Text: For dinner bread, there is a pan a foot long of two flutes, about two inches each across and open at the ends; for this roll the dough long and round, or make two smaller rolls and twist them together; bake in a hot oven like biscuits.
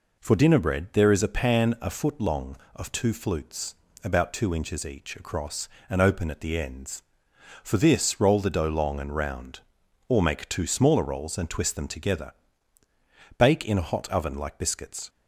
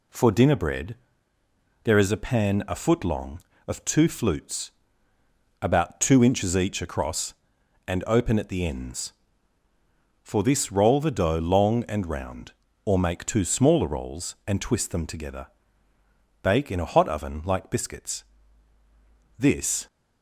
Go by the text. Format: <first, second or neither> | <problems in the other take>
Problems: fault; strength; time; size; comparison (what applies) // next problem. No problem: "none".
first | goes on to say "This"; slight; from 19.3 s on; 0.48 s long